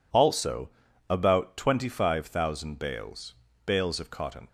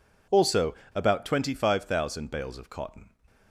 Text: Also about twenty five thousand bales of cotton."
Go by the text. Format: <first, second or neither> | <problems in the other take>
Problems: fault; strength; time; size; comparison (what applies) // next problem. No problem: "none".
second | pauses between "Also" and "about"; at 0.7 s; 0.38 s long; slight in the second // says "bales" twice; at 3.6 s